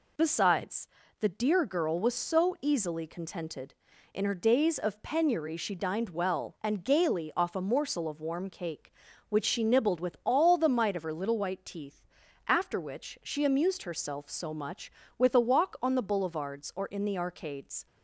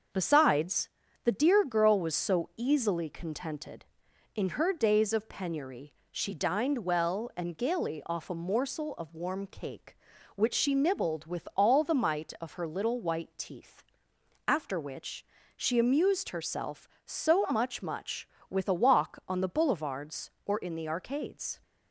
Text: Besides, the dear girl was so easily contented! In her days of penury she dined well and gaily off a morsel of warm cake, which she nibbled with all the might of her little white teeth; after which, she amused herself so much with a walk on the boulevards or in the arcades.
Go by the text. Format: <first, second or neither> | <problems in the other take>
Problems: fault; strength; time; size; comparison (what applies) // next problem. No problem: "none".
first | starts louder than the rest; until 1.4 s; 6.5 dB // pauses between "penury" and "she"; slight; at 5.9 s; 0.18 s long // says "much" twice; at 17.8 s